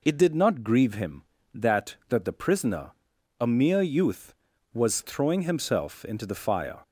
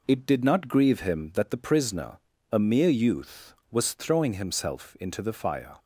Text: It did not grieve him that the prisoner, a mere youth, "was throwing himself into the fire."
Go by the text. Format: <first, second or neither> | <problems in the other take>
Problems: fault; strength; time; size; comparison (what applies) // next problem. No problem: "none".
second | says "that" twice; at 2.0 s